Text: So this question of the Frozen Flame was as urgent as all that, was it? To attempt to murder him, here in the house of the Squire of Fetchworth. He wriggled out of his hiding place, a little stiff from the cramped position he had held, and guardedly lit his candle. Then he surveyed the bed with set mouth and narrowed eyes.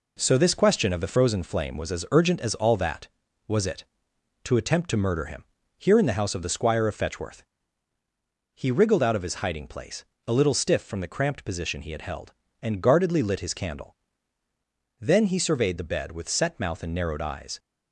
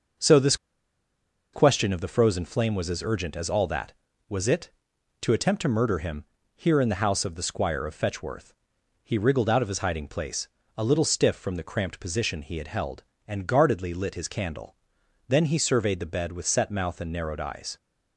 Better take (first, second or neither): first